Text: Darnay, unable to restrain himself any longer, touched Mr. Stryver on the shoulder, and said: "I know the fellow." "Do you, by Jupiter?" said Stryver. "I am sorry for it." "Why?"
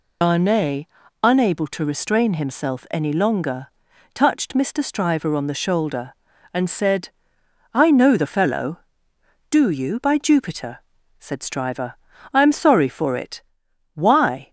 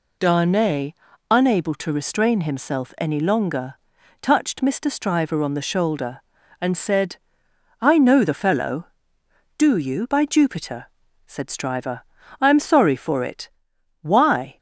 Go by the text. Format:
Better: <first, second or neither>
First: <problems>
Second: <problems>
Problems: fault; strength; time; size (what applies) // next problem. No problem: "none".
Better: second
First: loses the start of "Darnay"; at 0.2 s; 90 ms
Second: none